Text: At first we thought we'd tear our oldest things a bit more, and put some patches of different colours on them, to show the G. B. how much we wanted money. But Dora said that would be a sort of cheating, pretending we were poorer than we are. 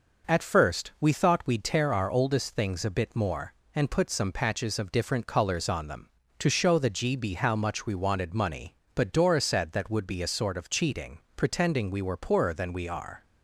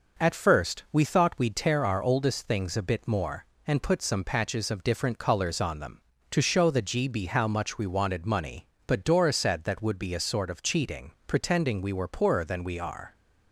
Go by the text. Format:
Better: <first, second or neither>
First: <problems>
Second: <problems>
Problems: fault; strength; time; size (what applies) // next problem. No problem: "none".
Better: neither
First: none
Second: none